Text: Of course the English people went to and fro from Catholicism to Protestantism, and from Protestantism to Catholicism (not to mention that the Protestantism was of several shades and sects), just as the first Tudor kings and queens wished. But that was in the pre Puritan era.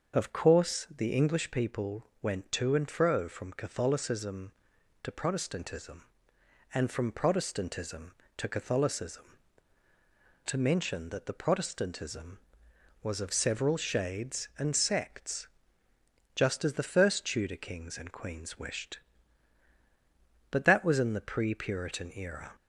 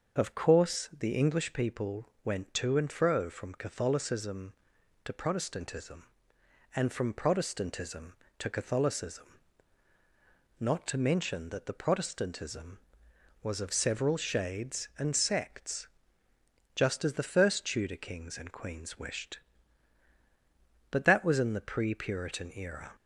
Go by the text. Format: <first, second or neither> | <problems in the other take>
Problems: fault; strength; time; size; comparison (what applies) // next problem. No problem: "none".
second | starts louder than the rest; until 1.2 s; 6.5 dB; also in the second // pauses between "people" and "went"; slight; at 2.0 s; 0.16 s long; slight in the second // skips "not"; at 9.8 s